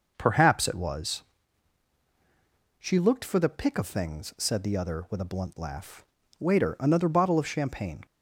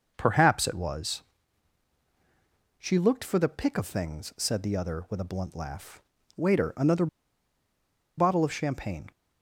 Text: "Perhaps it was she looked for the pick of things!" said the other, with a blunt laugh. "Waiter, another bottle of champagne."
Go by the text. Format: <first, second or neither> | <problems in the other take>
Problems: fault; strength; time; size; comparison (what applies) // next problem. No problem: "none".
first | pauses between "was" and "she"; strong; at 1.2 s; 1.5 s long; strong in the first // pauses between "another" and "bottle"; at 7.0 s; 1.1 s long